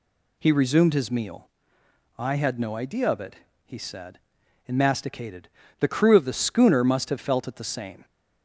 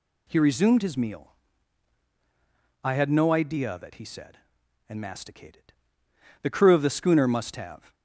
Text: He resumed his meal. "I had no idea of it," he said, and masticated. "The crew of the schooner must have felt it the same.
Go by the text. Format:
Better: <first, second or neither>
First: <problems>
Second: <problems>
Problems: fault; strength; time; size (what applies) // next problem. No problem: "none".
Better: first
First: none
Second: stops before "felt it the same"; at 7.9 s